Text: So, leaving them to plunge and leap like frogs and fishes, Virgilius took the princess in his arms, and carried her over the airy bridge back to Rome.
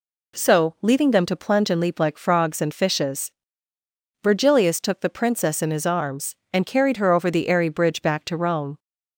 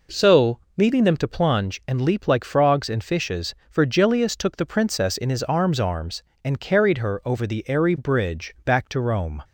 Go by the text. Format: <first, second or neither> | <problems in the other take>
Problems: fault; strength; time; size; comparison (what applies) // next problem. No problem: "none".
first | says "arms" twice; at 5.7 s